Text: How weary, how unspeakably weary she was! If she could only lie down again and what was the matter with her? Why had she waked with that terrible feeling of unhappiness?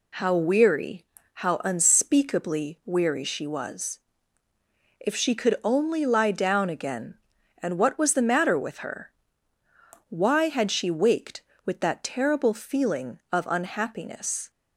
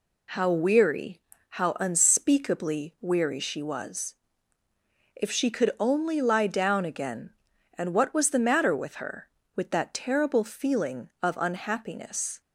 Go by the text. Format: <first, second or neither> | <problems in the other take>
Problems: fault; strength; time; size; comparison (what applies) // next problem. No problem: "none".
first | skips "Why had she waked"; at 9.4 s